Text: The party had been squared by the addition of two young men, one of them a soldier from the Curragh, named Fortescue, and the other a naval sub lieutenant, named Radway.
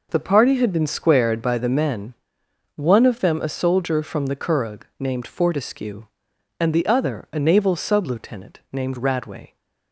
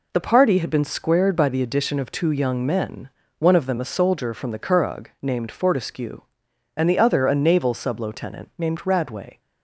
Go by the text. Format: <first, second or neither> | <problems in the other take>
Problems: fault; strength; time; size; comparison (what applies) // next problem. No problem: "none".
second | skips "addition of two young"; at 1.6 s